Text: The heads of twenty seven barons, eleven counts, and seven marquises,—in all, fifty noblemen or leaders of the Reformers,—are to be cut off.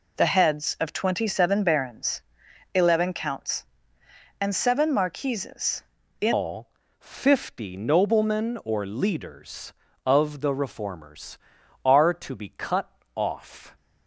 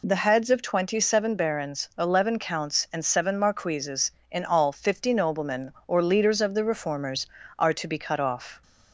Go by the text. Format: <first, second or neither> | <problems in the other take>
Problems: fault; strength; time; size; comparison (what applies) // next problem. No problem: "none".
second | changes voice at "all"; from 6.3 s on; 7.4 s long // pauses between "cut" and "off"; slight; at 12.9 s; 0.24 s long